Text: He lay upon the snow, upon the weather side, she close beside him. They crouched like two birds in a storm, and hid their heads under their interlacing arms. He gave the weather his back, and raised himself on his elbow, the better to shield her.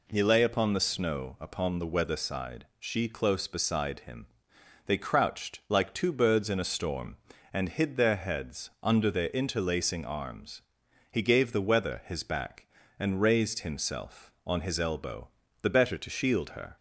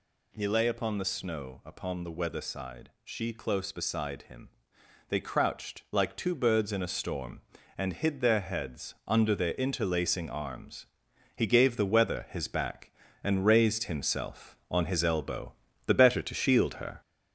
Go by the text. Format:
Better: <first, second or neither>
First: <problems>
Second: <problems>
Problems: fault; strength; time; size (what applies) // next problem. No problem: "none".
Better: first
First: none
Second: gets louder; noticeable; throughout; 4.5 dB